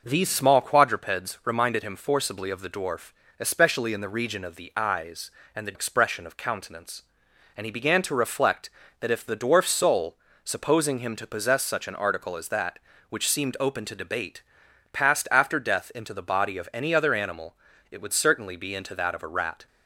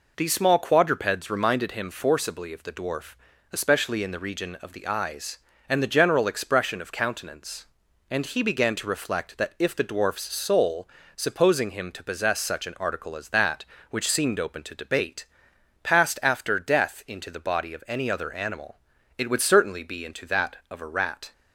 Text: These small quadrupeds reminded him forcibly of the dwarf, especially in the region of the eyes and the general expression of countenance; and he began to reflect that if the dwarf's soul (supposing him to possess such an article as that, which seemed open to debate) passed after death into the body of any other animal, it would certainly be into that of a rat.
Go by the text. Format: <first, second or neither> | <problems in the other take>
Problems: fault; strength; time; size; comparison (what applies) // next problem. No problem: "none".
second | skips "general"; at 5.7 s